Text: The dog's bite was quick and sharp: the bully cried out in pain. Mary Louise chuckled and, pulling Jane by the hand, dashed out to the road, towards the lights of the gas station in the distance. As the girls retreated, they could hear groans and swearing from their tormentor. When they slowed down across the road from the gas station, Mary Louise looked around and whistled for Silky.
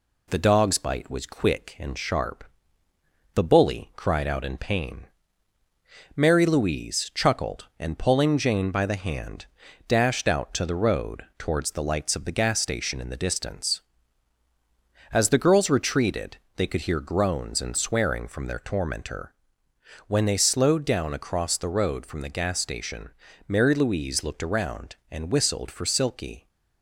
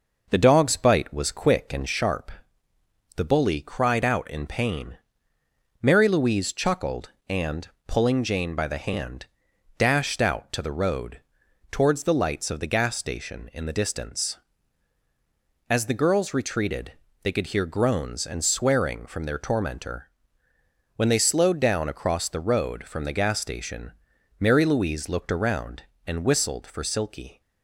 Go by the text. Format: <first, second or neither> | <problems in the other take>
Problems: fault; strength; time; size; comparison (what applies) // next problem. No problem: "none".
first | starts louder than the rest; noticeable; until 1.9 s; 5.5 dB